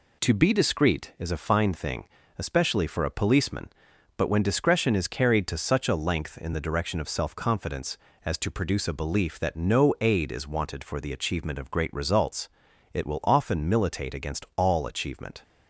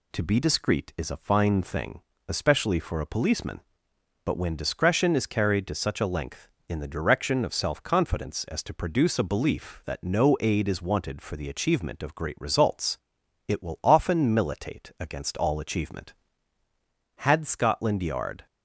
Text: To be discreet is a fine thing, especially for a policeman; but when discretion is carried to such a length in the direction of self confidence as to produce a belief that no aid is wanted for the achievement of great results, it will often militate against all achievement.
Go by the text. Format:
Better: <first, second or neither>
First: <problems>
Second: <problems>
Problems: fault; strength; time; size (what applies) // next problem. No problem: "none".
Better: first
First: none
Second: goes on to say "Had Scotland Yard"; noticeable; from 17.1 s on; 1.2 s long